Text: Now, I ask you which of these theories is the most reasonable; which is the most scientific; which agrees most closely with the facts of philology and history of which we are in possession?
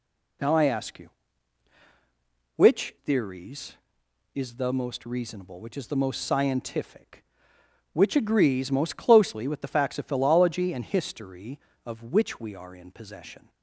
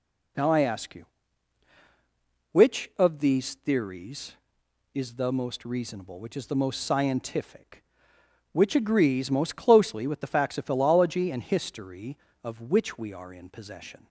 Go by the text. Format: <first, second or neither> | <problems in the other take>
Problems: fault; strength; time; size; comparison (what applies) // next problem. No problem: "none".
second | skips "of these"; at 2.9 s